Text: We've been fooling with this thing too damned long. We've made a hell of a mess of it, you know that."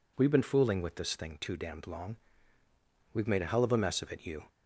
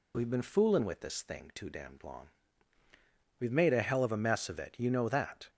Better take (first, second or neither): second